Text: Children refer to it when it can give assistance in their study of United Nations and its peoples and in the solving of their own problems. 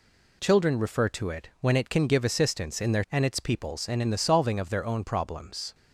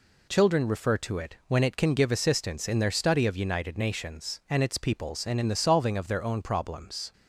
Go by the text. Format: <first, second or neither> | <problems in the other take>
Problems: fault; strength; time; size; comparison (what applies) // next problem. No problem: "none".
second | skips "study of United Nations"; at 3.0 s